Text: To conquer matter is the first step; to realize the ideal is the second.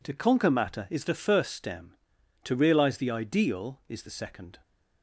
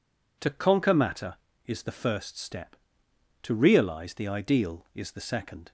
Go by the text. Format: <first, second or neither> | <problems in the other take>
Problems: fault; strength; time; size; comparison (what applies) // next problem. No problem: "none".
second | says "stem" for "step"; at 1.5 s